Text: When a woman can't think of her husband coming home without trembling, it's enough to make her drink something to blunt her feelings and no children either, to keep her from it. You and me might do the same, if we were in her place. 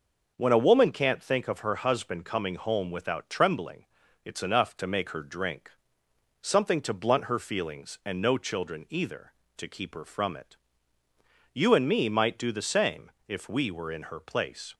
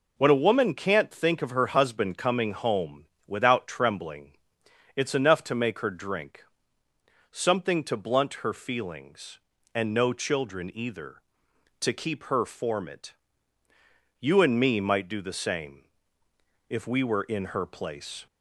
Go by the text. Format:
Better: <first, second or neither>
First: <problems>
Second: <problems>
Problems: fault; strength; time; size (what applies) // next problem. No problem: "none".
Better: first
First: pauses between "drink" and "something"; noticeable; at 5.6 s; 0.72 s long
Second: pauses between "home" and "without"; slight; at 3.0 s; 0.22 s long // pauses between "drink" and "something"; noticeable; at 6.4 s; 0.86 s long // says "form" for "from"; at 12.4 s